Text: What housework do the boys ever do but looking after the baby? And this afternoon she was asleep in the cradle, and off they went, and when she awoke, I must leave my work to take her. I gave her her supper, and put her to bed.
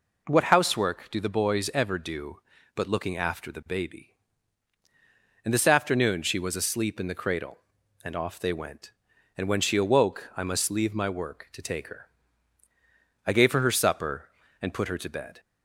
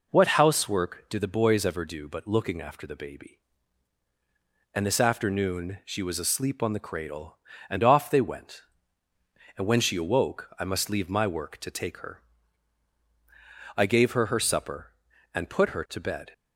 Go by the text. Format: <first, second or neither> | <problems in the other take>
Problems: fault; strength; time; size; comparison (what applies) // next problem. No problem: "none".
first | says "on" for "in"; at 6.6 s